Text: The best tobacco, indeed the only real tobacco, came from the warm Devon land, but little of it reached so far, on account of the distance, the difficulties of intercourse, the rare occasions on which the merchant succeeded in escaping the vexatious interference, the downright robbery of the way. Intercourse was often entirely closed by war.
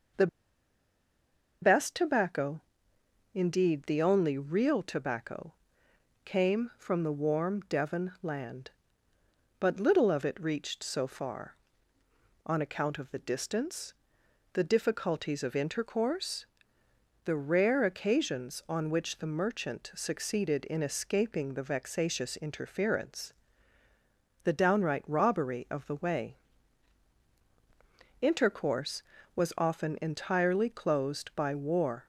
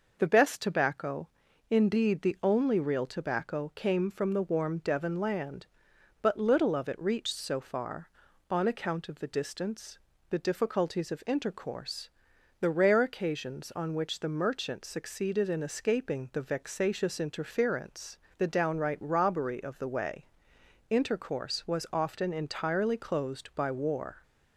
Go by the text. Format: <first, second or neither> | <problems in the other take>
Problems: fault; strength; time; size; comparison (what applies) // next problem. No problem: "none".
second | pauses between "The" and "best"; strong; at 0.2 s; 1.3 s long